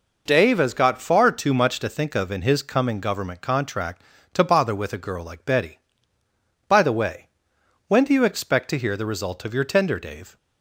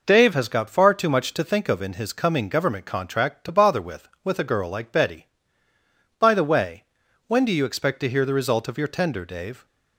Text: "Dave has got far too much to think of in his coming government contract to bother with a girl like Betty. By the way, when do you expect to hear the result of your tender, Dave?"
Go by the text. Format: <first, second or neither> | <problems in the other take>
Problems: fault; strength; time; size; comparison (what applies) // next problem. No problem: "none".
first | says "with" twice; at 4.2 s